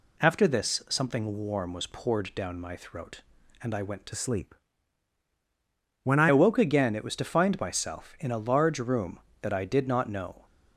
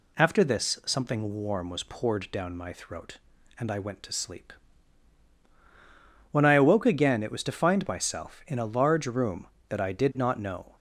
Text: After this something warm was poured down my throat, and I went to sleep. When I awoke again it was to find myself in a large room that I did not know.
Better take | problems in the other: second | changes voice from "sleep" to "I"; from 4.1 to 6.2 s; 2.1 s long

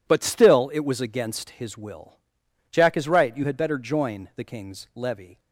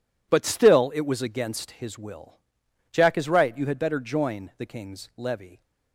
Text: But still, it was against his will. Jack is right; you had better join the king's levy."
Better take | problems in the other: neither | none

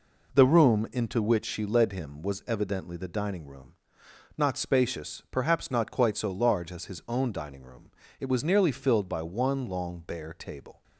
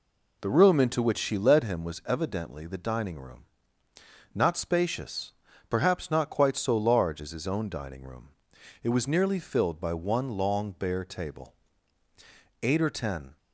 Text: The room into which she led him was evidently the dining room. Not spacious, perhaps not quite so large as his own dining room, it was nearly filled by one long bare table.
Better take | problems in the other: first | goes on to say "Eight or ten"; noticeable; from 12.6 s on; 0.76 s long

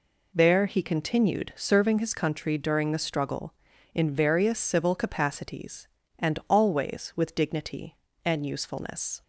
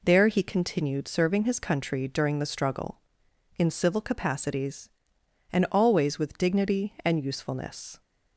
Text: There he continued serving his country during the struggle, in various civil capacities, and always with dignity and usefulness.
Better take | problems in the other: first | skips "various"; at 3.6 s

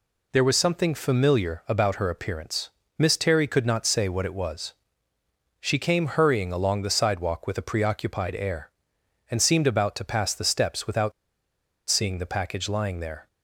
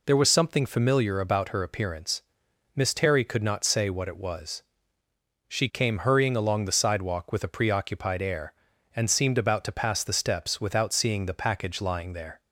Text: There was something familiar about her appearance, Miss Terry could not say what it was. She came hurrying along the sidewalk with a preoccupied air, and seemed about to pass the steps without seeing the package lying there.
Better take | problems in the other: second | pauses between "without" and "seeing"; noticeable; at 11.1 s; 0.77 s long

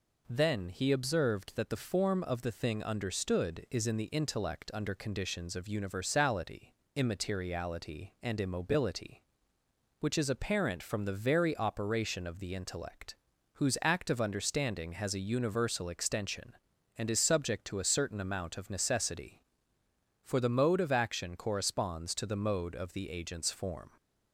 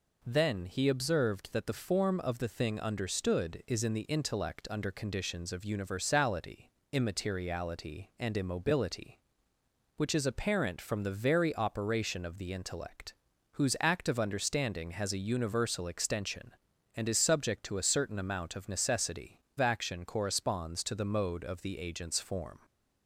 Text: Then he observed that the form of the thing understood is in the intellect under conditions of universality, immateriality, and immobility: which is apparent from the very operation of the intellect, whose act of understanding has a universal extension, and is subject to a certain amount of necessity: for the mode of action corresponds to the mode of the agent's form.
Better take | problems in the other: first | skips "for the mode of"; at 19.4 s

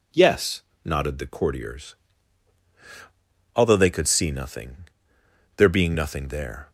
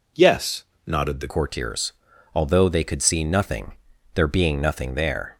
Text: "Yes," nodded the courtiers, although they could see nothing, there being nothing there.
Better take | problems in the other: first | changes voice at "courtiers"; from 1.2 s on; 4.1 s long

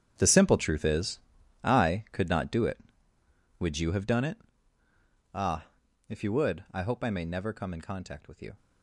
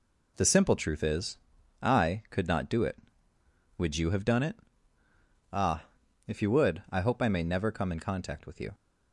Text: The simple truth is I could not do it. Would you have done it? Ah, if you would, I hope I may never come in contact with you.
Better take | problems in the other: second | gets quieter; strong; throughout; 14.5 dB // pauses between "is" and "I"; at 1.1 s; 0.42 s long; also in the second

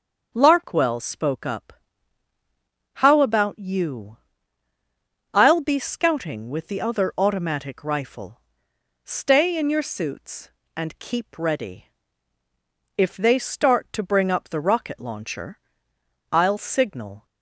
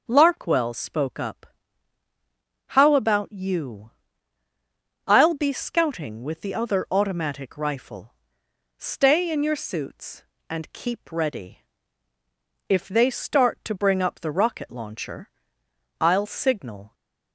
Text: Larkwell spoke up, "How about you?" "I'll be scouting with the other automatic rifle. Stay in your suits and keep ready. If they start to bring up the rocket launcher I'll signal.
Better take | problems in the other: neither | starts louder than the rest; the same in both // pauses between "launcher" and "I'll"; noticeable; the same in both

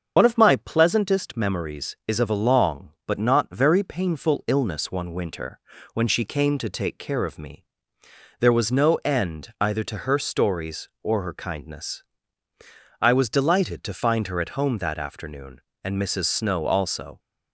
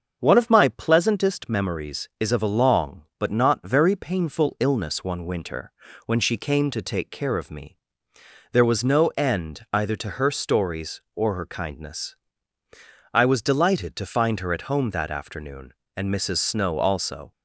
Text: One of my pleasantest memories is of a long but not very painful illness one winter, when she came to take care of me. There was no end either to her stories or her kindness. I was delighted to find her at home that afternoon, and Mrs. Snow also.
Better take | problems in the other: second | loses the start of "One"; at 0.1 s; 75 ms // starts louder than the rest; until 1.1 s; 7 dB; also in the second

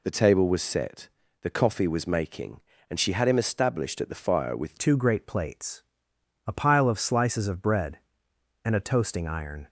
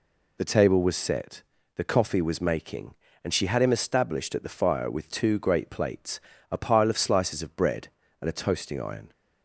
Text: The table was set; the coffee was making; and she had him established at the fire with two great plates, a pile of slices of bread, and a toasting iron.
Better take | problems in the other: second | changes voice at "two"; from 4.7 s on; 4.9 s long

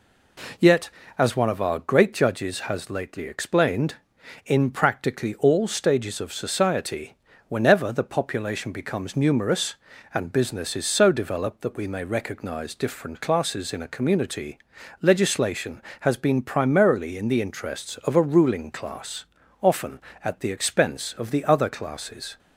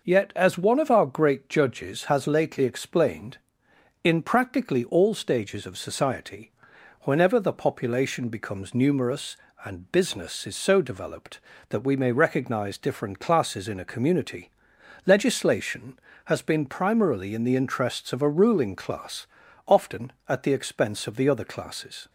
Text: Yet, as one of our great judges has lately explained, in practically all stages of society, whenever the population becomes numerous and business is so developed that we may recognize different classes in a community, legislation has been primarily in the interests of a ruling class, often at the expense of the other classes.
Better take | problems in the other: neither | none

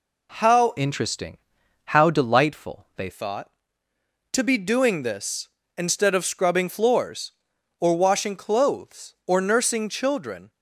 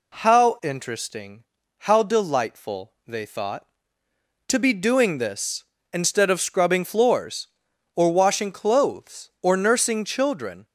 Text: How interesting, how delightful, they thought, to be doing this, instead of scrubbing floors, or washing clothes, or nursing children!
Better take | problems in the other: second | changes voice from "interesting" to "they"; from 0.7 to 3.0 s; 2.3 s long

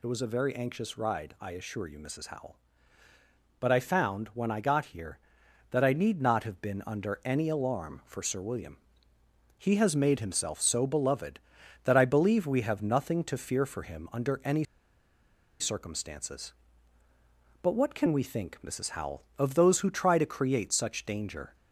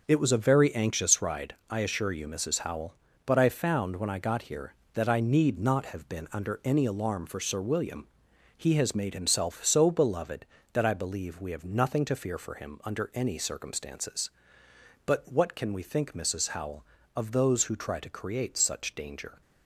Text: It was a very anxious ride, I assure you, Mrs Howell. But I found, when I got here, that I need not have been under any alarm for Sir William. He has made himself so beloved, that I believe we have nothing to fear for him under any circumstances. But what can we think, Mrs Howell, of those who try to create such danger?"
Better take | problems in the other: second | pauses between "any" and "circumstances"; noticeable; at 14.6 s; 0.96 s long

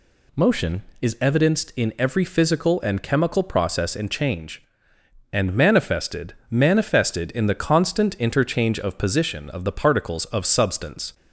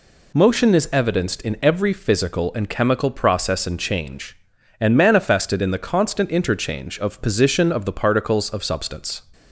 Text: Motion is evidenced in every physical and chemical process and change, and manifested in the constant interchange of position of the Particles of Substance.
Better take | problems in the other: second | says "manifested" twice; at 6.5 s

